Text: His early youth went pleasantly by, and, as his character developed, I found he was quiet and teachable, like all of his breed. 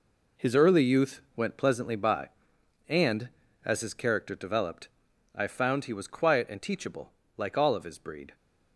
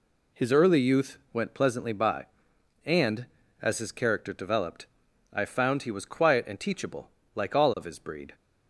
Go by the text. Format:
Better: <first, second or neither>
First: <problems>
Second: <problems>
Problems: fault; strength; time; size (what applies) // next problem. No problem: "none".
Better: second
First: gets quieter; strong; throughout; 10 dB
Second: none